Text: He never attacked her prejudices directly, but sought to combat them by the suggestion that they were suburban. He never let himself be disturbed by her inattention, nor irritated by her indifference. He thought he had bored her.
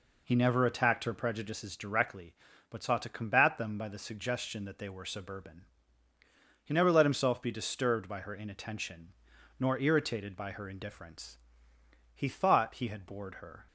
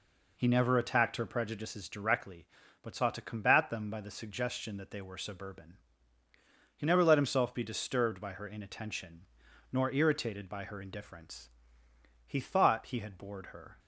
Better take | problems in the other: neither | none

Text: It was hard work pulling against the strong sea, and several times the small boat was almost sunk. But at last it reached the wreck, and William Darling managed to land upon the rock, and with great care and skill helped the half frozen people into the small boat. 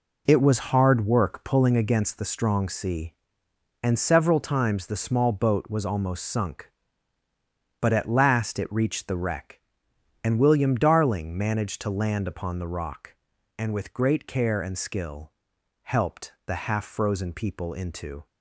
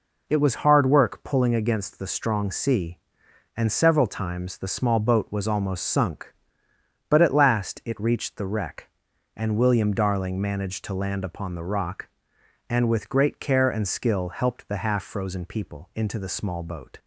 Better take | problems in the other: second | pauses between "skill" and "helped"; noticeable; at 15.3 s; 0.54 s long // stops before "the small boat"; at 18.2 s

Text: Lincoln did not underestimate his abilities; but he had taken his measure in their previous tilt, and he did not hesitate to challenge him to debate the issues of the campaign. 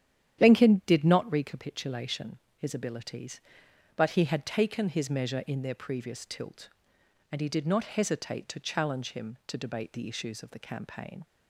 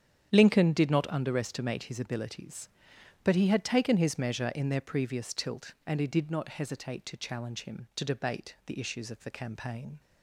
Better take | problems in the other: second | starts louder than the rest; strong; until 1.4 s; 10 dB; strong in the second // says "recapitulation" for "underestimate"; at 1.2 s

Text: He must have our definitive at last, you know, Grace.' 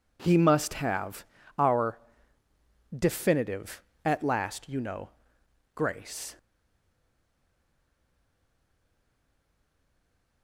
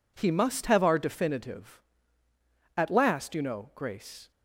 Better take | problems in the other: second | pauses between "have" and "our"; slight; at 1.2 s; 0.32 s long // pauses between "our" and "definitive"; at 1.9 s; 1.0 s long // stays silent after the last word; strong; from 6.3 s on; 4.1 s long

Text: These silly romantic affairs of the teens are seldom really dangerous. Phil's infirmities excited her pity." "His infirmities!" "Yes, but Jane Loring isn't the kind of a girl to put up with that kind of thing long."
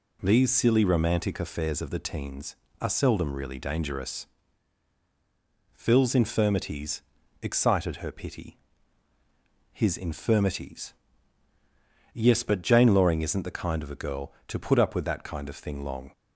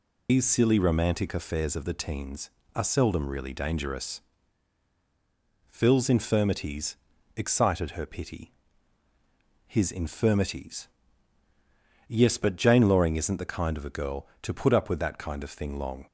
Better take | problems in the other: first | loses the start of "These"; at 0.2 s; 140 ms // pauses between "infirmities" and "excited"; at 6.9 s; 0.40 s long; also in the first

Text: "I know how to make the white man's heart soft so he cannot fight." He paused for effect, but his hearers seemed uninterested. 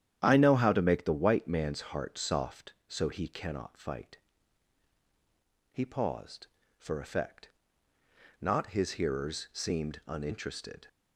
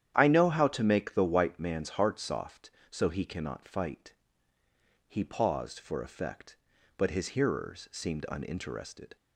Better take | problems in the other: second | starts louder than the rest; strong; until 1.2 s; 10 dB; strong in the second // says "not" for "but"; at 8.4 s

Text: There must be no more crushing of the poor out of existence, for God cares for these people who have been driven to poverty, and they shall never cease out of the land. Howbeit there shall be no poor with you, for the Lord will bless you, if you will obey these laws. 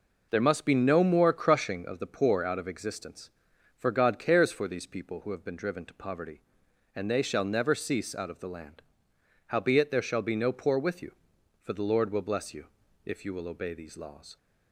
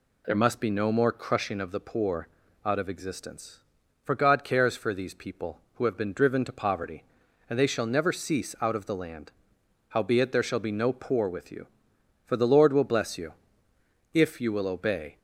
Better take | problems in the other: first | pauses between "poor" and "out"; slight; at 2.2 s; 0.36 s long // stops before "these laws"; at 15.1 s

